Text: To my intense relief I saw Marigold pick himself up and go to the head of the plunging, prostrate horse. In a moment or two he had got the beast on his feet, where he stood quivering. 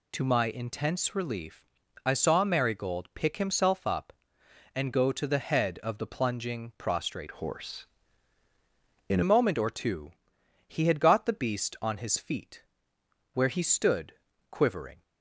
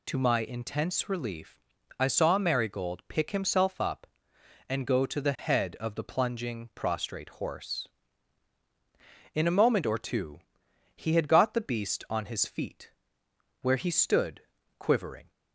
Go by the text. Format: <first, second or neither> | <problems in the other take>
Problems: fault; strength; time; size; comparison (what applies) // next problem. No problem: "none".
second | pauses between "relief" and "I"; slight; at 1.6 s; 0.36 s long; slight in the second // changes voice from "horse" to "In"; from 7.3 to 9.2 s; 1.9 s long // pauses between "two" and "he"; noticeable; at 10.1 s; 0.54 s long; noticeable in the second // pauses between "stood" and "quivering"; slight; at 14.1 s; 0.36 s long; slight in the second